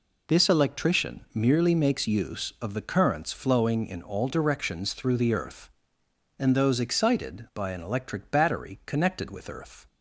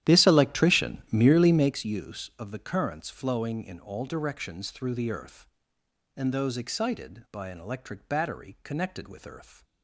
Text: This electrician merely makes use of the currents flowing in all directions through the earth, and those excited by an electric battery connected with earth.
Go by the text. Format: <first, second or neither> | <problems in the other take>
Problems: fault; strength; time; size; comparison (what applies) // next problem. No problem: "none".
first | starts louder than the rest; strong; until 1.8 s; 11.5 dB // pauses between "electrician" and "merely"; slight; at 0.9 s; 0.16 s long; slight in the first